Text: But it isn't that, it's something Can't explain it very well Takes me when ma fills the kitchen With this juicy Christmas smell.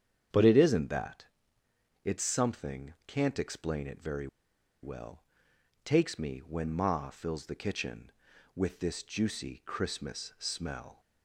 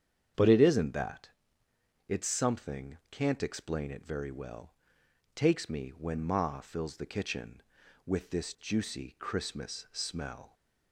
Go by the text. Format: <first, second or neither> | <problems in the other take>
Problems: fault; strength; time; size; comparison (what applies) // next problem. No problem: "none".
second | starts louder than the rest; strong; until 2.1 s; 8.5 dB; strong in the second // pauses between "very" and "well"; noticeable; at 4.2 s; 0.56 s long // pauses between "well" and "Takes"; noticeable; at 5.2 s; 0.62 s long; noticeable in the second